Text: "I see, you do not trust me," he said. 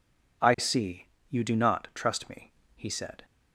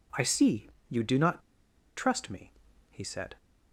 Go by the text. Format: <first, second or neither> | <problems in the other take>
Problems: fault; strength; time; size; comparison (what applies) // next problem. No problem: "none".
first | pauses between "not" and "trust"; noticeable; at 1.3 s; 0.58 s long